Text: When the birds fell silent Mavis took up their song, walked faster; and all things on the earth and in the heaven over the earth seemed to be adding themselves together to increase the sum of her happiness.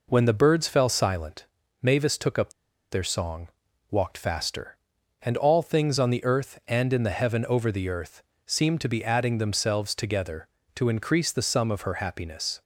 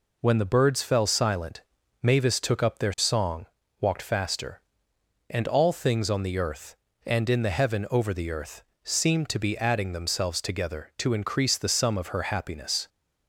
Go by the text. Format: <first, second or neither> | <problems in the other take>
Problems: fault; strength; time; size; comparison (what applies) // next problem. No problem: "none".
second | pauses between "silent" and "Mavis"; at 1.4 s; 0.38 s long; also in the second // pauses between "up" and "their"; at 2.5 s; 0.39 s long // pauses between "earth" and "seemed"; slight; at 8.2 s; 0.24 s long; slight in the second